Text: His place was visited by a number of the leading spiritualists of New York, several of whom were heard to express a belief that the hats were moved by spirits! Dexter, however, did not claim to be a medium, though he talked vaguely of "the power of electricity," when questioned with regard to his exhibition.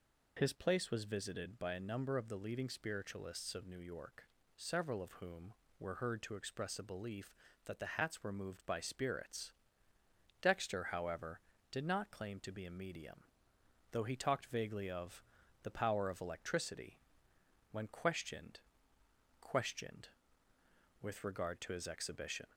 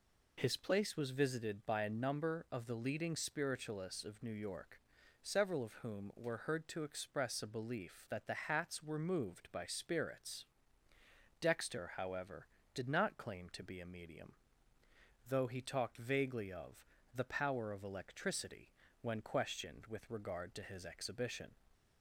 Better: second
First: pauses between "of" and "the"; at 15.2 s; 0.40 s long // says "questioned" twice; at 19.3 s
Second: pauses between "of" and "the"; slight; at 16.8 s; 0.28 s long

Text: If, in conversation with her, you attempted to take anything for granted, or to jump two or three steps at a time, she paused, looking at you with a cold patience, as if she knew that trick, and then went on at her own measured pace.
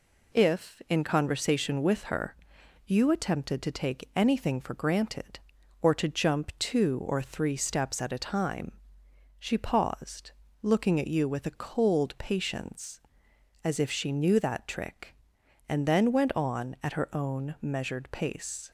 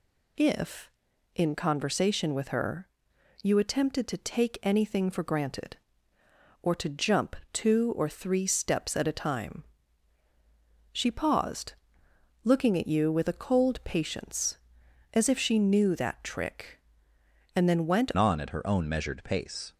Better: first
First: none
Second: pauses between "jump" and "two"; slight; at 7.3 s; 0.16 s long // changes voice at "on"; from 18.1 s on; 1.6 s long

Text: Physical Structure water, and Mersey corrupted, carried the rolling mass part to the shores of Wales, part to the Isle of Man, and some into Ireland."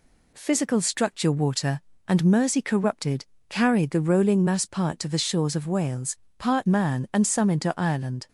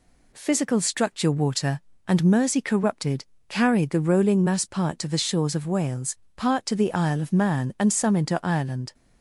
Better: second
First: skips "to the Isle of"; at 6.6 s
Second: none

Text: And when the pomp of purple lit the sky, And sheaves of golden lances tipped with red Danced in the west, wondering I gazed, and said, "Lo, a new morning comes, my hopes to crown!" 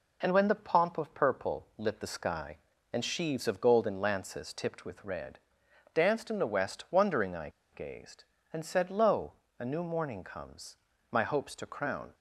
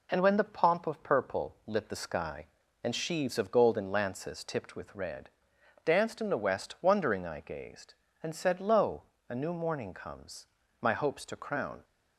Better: second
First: pauses between "red" and "Danced"; noticeable; at 5.3 s; 0.56 s long // pauses between "I" and "gazed"; slight; at 7.4 s; 0.23 s long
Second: pauses between "red" and "Danced"; noticeable; at 5.2 s; 0.56 s long

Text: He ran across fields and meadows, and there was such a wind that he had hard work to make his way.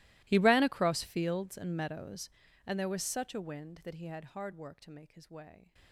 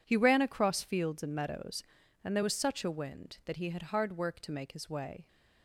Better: second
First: gets quieter; strong; throughout; 24 dB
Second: none

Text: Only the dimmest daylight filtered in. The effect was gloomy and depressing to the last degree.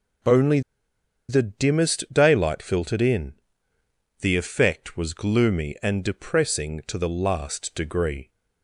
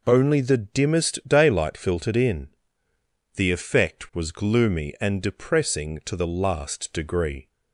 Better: second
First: pauses between "Only" and "the"; noticeable; at 0.5 s; 0.68 s long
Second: none

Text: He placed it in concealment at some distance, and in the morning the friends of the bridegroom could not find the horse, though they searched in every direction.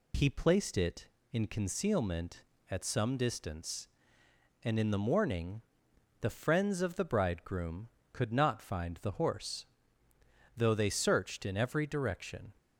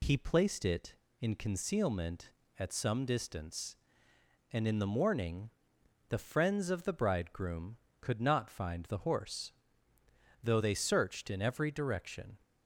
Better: neither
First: pauses between "morning" and "the"; noticeable; at 5.6 s; 0.60 s long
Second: pauses between "morning" and "the"; noticeable; at 5.4 s; 0.60 s long

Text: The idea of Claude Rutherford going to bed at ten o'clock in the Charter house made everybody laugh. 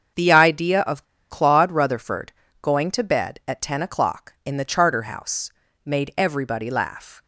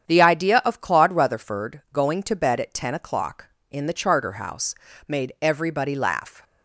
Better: second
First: starts louder than the rest; until 1.4 s; 7 dB // pauses between "of" and "Claude"; slight; at 1.0 s; 0.24 s long // pauses between "Rutherford" and "going"; slight; at 2.3 s; 0.30 s long // pauses between "house" and "made"; slight; at 5.5 s; 0.34 s long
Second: starts louder than the rest; strong; until 1.1 s; 8.5 dB // pauses between "house" and "made"; slight; at 4.7 s; 0.32 s long

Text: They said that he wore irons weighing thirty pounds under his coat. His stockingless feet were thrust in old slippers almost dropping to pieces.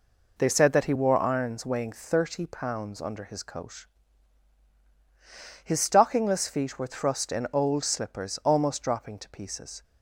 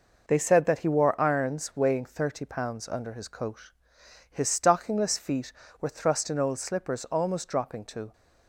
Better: first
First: none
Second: stops before "pieces"; at 8.1 s

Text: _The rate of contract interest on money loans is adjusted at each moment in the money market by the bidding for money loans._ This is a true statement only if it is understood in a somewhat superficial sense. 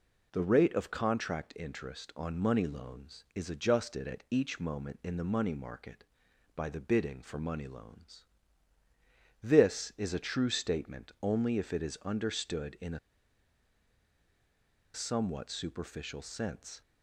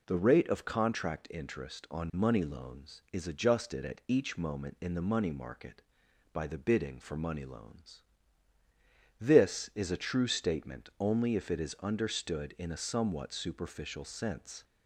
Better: second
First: pauses between "a" and "somewhat"; strong; at 12.9 s; 1.9 s long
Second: none

